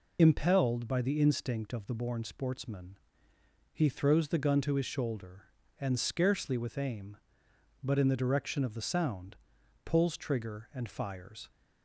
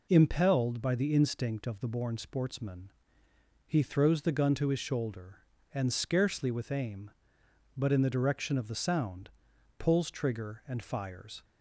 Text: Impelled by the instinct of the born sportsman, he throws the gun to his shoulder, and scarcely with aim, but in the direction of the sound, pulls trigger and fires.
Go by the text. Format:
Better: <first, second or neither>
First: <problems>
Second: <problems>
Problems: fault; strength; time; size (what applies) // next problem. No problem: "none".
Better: second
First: loses the start of "Impelled"; at 0.1 s; 35 ms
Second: none